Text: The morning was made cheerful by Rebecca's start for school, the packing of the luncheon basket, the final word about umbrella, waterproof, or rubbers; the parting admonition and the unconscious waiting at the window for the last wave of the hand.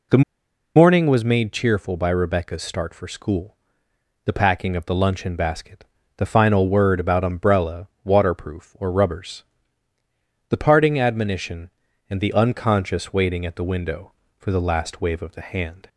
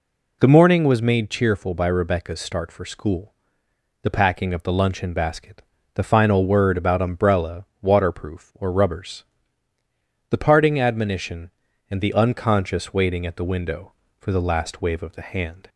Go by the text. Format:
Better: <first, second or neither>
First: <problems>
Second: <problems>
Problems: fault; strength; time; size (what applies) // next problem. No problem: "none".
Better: second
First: pauses between "The" and "morning"; noticeable; at 0.2 s; 0.54 s long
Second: none